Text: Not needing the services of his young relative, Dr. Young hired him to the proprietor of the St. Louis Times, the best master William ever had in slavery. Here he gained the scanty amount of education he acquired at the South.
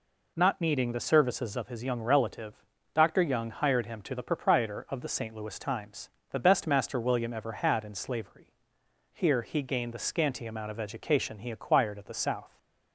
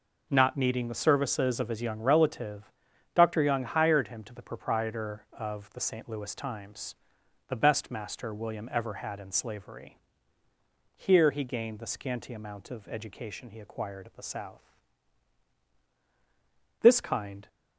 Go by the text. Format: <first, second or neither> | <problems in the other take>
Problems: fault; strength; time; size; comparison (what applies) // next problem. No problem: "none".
first | goes on to say "This kind"; noticeable; from 16.8 s on; 0.66 s long